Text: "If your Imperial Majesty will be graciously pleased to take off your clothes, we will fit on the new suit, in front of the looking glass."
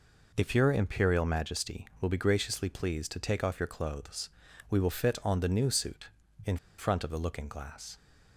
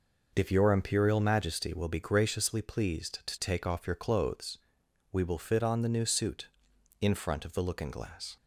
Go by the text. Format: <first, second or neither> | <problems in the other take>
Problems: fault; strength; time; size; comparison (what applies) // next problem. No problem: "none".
second | pauses between "in" and "front"; slight; at 6.5 s; 0.21 s long